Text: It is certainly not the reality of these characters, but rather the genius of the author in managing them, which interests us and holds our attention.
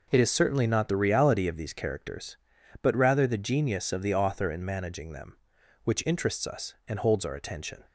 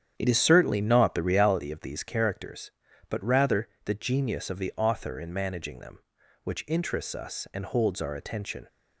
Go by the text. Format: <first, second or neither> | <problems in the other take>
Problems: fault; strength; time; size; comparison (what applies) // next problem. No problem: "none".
first | starts louder than the rest; strong; until 1.5 s; 9 dB // pauses between "rather" and "the"; slight; at 3.6 s; 0.16 s long